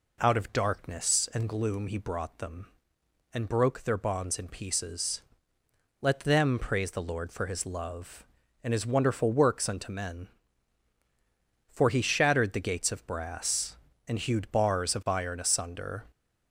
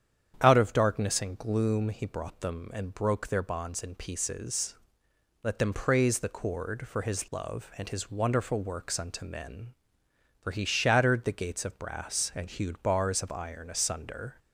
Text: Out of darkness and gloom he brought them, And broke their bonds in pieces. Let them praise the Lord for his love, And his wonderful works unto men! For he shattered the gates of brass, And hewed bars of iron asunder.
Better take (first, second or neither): first